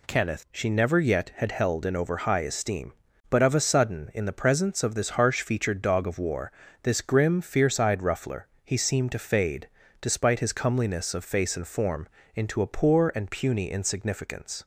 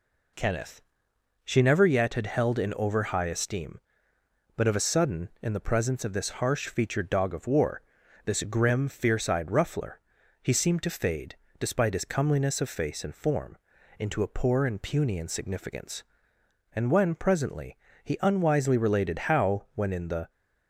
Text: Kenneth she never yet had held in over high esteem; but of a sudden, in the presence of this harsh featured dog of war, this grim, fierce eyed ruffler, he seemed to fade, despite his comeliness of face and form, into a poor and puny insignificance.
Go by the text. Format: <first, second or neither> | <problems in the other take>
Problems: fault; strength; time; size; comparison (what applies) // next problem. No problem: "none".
first | pauses between "Kenneth" and "she"; noticeable; at 0.8 s; 0.62 s long // goes on to say "And when presently he unwisely related how when in the"; strong; from 16.7 s on; 3.5 s long